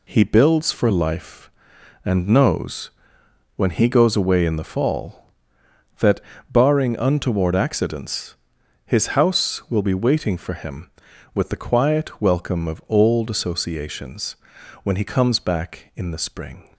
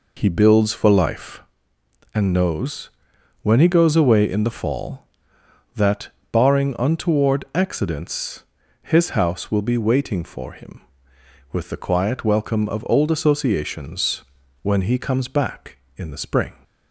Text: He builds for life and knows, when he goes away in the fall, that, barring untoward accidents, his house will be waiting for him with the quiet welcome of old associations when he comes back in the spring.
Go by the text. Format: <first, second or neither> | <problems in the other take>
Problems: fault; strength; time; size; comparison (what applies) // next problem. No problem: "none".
first | starts louder than the rest; noticeable; until 1.5 s; 4 dB // pauses between "associations" and "when"; at 14.2 s; 0.40 s long; noticeable in the first